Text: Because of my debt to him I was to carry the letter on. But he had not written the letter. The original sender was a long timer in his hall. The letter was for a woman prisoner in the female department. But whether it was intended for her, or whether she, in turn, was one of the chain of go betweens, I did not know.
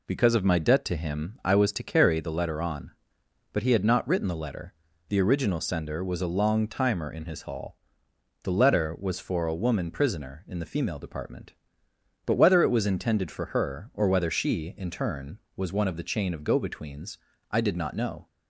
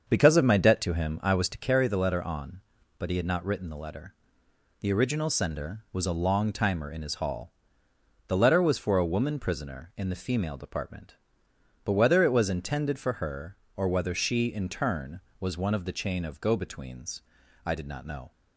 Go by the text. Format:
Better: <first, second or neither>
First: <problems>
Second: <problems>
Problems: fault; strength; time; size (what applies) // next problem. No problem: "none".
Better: first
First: none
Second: starts louder than the rest; until 1.6 s; 6.5 dB